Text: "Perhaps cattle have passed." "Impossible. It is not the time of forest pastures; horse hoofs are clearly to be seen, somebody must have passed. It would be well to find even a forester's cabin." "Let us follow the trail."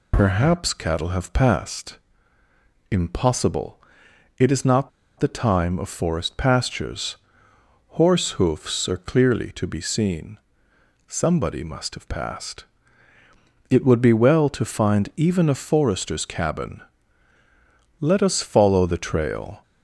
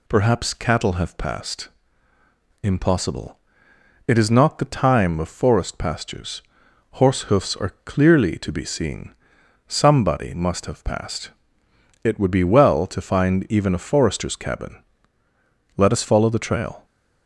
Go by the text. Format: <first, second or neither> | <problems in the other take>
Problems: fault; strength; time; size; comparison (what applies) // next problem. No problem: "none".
second | pauses between "not" and "the"; slight; at 4.8 s; 0.30 s long